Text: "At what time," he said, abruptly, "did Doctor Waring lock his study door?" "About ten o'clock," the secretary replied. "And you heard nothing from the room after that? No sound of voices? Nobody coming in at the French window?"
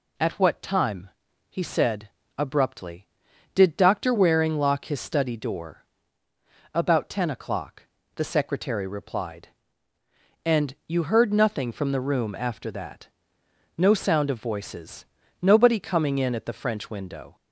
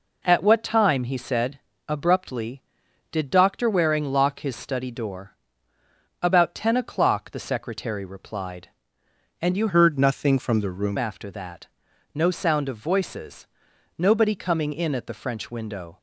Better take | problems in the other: first | changes voice from "heard" to "room"; from 9.6 to 10.9 s; 1.3 s long

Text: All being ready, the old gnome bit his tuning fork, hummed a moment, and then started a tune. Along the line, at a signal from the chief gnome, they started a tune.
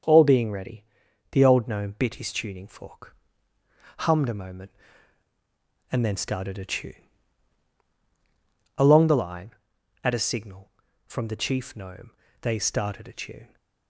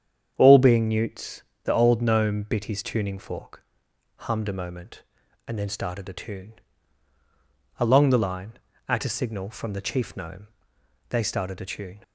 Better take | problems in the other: first | starts louder than the rest; strong; until 1.3 s; 8 dB; strong in the first // says "newts" for "ready"; at 0.8 s

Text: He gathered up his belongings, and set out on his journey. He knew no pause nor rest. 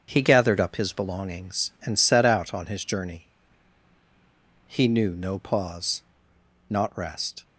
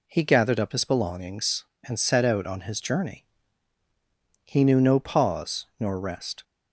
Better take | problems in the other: second | starts louder than the rest; strong; until 1.0 s; 7 dB // says "not" for "nor"; at 6.6 s

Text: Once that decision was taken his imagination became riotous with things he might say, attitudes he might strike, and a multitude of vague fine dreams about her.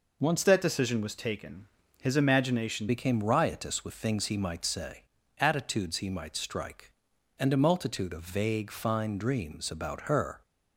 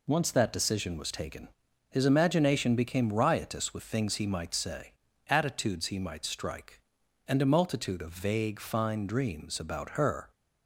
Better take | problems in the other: second | changes voice from "that" to "imagination"; from 0.4 to 2.8 s; 2.4 s long // pauses between "taken" and "his"; slight; at 1.6 s; 0.36 s long; also in the second

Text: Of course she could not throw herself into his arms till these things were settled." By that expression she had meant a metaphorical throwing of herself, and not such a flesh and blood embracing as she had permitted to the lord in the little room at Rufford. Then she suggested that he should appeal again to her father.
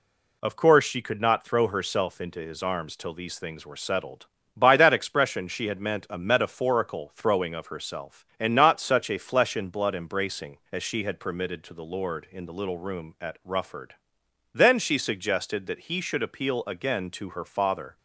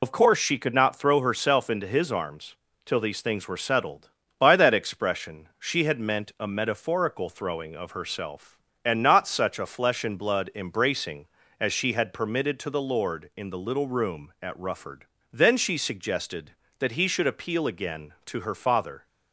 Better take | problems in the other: first | loses the start of "Of"; at 0.0 s; 55 ms // pauses between "arms" and "till"; slight; at 2.5 s; 0.28 s long

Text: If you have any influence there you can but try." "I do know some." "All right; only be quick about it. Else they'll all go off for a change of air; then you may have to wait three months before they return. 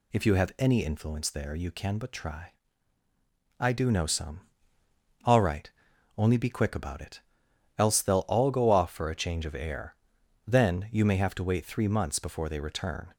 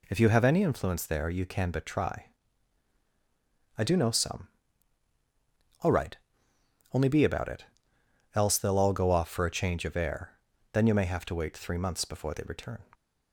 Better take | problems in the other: first | skips "quick"; at 7.2 s

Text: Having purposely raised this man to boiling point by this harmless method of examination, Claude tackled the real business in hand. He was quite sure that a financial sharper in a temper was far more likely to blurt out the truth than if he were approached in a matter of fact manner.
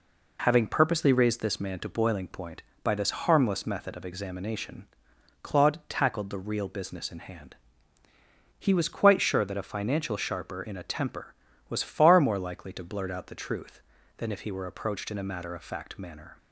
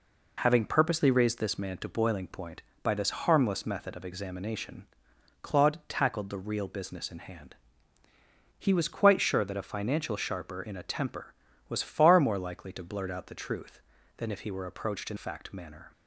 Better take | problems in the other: first | skips "a matter of"; at 15.1 s

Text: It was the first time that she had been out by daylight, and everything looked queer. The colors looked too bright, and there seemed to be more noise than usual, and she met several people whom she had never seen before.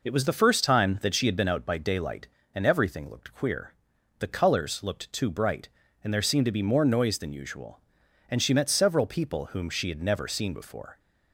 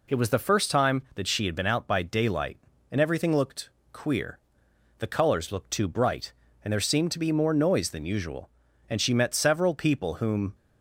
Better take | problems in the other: first | pauses between "looked" and "queer"; slight; at 3.6 s; 0.24 s long // stops before "she had never seen before"; at 10.5 s

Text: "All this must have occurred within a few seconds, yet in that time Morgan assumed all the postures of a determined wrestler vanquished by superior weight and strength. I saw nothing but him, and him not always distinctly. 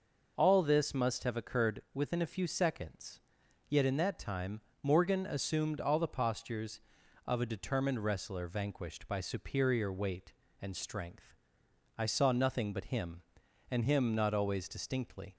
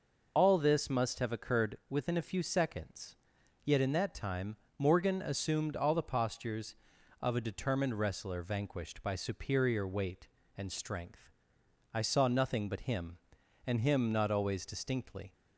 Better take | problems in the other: first | loses the start of "All"; at 0.3 s; 30 ms // pauses between "time" and "Morgan"; slight; at 4.5 s; 0.20 s long; slight in the first

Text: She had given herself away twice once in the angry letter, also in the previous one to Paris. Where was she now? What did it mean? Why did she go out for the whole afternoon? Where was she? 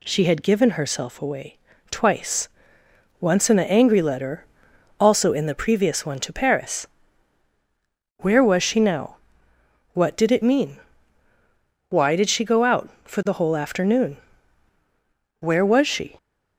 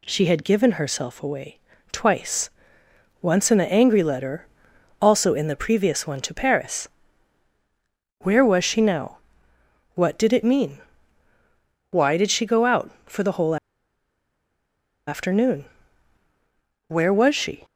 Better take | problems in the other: first | pauses between "away" and "twice"; slight; at 1.5 s; 0.34 s long; slight in the first // pauses between "twice" and "once"; noticeable; at 2.4 s; 0.72 s long; noticeable in the first // pauses between "whole" and "afternoon"; strong; at 13.5 s; 1.5 s long

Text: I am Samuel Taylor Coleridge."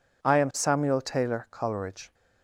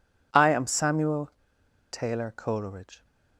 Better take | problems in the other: first | pauses between "Samuel" and "Taylor"; noticeable; at 1.2 s; 0.63 s long

